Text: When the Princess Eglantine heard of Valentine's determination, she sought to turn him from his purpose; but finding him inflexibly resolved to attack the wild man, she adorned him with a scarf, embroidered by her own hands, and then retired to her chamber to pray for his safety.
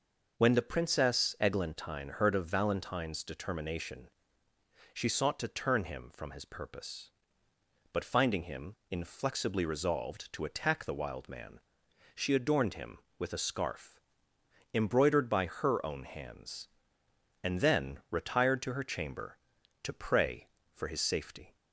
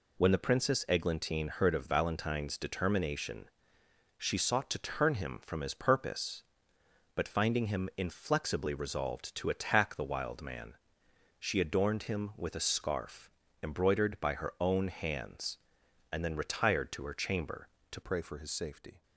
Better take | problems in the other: first | changes voice at "pray"; from 18.0 s on; 1.0 s long

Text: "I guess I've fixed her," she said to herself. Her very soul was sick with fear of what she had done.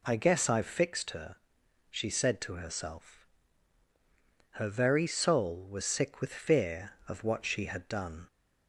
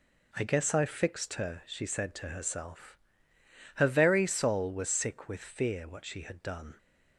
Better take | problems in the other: first | skips "of"; at 5.8 s

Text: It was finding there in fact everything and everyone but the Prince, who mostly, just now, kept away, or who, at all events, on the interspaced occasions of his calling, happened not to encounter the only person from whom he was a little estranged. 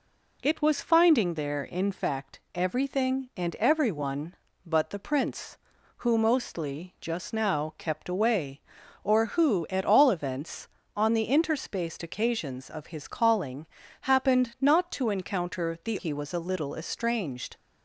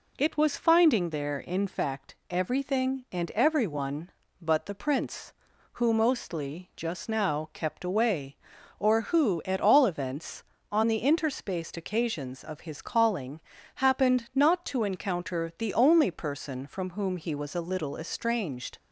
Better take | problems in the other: second | pauses between "fact" and "everything"; slight; at 2.3 s; 0.16 s long; slight in the second // skips "only person from whom"; at 15.9 s

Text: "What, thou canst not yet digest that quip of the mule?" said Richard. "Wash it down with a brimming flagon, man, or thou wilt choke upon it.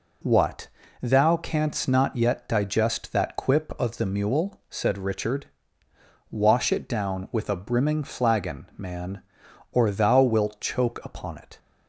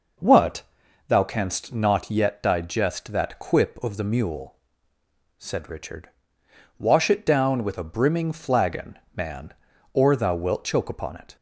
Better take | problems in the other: neither | none

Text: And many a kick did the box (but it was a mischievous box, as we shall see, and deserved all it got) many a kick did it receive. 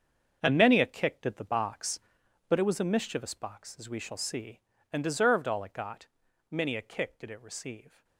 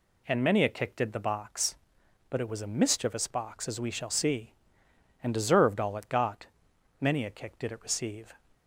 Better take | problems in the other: second | gets quieter; strong; throughout; 12 dB

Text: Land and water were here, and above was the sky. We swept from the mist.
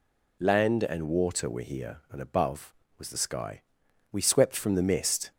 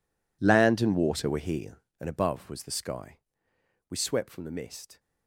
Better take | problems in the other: first | gets quieter; strong; throughout; 18 dB

